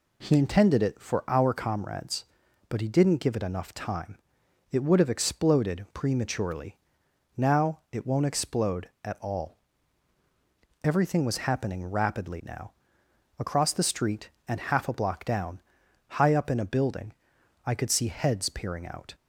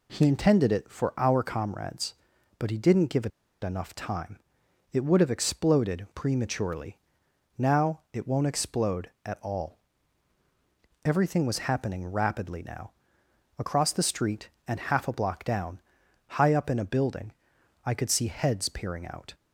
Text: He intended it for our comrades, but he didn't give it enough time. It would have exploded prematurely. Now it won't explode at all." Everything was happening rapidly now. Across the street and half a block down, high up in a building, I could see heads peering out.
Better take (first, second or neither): first